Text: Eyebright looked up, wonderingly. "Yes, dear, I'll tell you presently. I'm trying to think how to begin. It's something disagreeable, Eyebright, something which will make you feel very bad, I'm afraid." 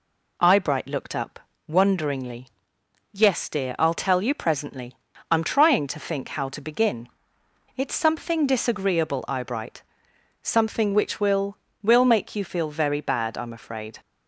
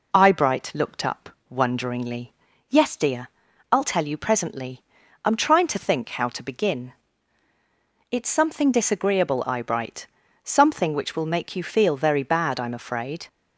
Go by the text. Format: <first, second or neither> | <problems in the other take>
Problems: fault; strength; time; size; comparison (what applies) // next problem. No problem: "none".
second | says "will" twice; at 11.8 s